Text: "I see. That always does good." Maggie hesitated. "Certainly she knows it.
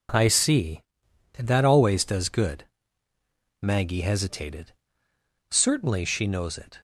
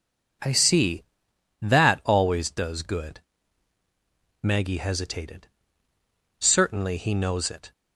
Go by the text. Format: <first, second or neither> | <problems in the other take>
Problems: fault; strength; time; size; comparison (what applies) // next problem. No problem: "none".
first | says "he" for "she"; at 6.9 s